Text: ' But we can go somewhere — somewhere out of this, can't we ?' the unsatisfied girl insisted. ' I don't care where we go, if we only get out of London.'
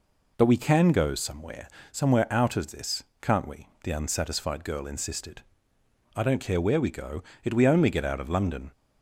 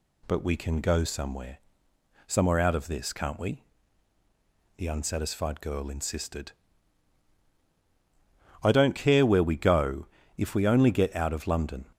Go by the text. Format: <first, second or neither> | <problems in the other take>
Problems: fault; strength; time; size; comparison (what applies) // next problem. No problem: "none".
second | says "it" for "if"; at 7.4 s